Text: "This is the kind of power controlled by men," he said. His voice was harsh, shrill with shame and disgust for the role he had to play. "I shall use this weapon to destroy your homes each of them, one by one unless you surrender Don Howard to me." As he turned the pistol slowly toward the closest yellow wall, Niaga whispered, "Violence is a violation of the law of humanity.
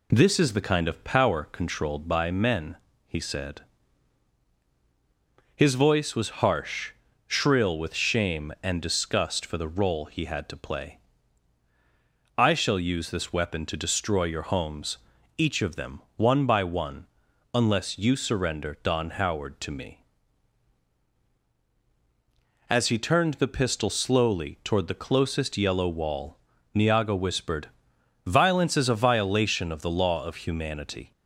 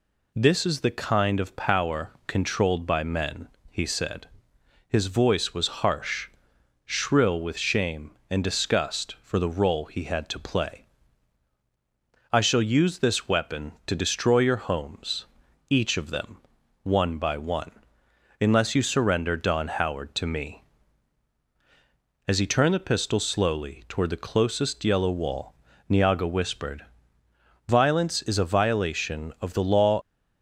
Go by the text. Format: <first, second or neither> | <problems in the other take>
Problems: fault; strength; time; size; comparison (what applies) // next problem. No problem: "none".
first | pauses between "homes" and "each"; at 15.2 s; 0.42 s long; also in the first // pauses between "one" and "unless"; noticeable; at 17.7 s; 0.70 s long; noticeable in the first // stops before "of humanity"; at 30.0 s